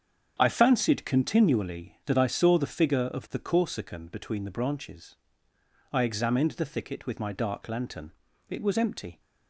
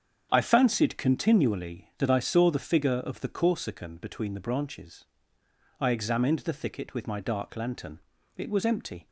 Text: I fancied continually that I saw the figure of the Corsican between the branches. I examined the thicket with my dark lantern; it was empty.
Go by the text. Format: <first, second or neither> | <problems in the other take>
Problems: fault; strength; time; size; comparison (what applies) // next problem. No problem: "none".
neither | starts louder than the rest; strong; the same in both